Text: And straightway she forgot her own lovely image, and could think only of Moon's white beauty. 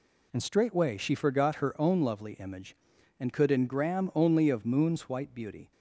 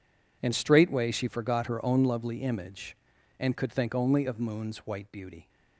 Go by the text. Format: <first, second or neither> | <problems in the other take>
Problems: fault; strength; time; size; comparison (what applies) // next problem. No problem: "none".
second | says "engram" for "think"; at 3.4 s